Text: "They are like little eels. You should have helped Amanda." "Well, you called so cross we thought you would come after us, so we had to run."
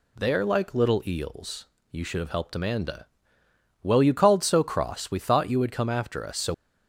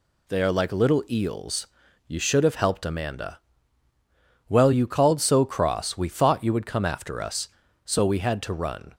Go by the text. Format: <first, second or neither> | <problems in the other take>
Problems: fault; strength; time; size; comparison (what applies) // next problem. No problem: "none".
second | stops before "we had to run"; at 6.5 s